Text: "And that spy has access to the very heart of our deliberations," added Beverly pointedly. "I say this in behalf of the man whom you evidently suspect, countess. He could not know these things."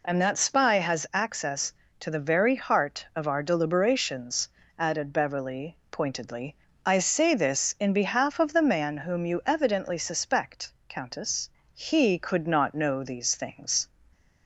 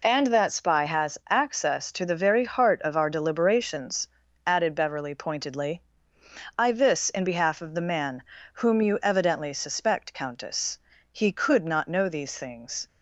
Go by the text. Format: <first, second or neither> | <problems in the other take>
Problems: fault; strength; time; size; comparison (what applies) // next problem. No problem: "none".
first | skips "say"; at 6.7 s // pauses between "man" and "whom"; slight; at 8.2 s; 0.34 s long